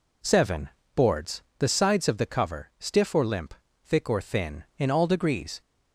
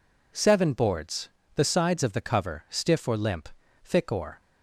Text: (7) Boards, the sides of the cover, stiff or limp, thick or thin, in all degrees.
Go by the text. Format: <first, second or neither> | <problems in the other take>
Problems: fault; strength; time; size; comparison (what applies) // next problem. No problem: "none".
first | stops before "thin in all degrees"; at 4.4 s